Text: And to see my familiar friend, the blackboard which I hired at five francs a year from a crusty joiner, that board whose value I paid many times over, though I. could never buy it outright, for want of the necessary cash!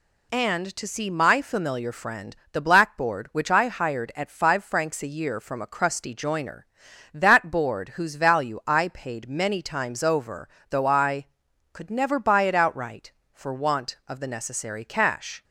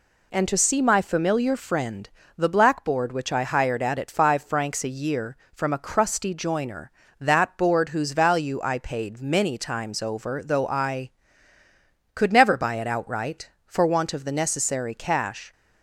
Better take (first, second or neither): first